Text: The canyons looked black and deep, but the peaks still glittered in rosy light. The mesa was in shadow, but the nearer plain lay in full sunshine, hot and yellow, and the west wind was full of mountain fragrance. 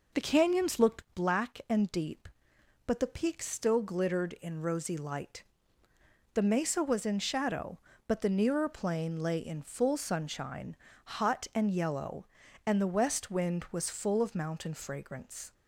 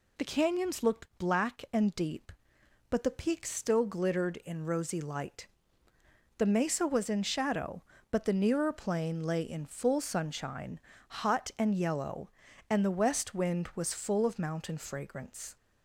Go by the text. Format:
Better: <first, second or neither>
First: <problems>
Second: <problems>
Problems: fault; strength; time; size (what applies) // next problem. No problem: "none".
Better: second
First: starts louder than the rest; noticeable; until 1.1 s; 5 dB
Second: none